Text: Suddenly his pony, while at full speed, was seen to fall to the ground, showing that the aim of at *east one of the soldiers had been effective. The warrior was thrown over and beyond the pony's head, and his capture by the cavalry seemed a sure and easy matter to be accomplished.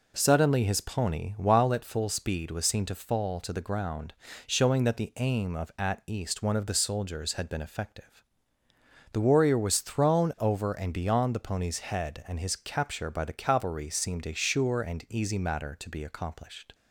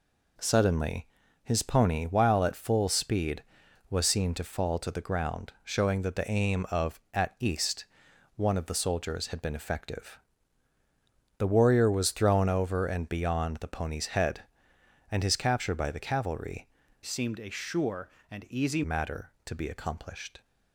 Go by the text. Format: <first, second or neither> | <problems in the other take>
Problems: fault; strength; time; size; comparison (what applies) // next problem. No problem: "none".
first | pauses between "Suddenly" and "his"; slight; at 1.0 s; 0.36 s long // pauses between "east" and "one"; noticeable; at 7.8 s; 0.50 s long // changes voice from "seemed" to "easy"; from 17.0 to 18.8 s; 1.8 s long